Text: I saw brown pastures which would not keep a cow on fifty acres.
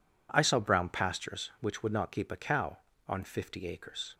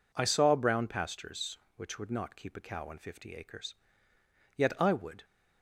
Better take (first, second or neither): first